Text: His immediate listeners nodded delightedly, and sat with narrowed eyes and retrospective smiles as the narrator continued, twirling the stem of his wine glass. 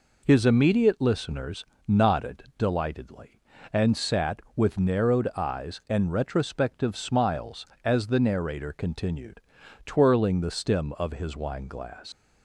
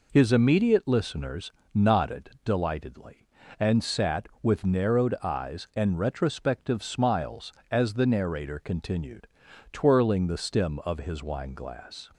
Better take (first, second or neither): second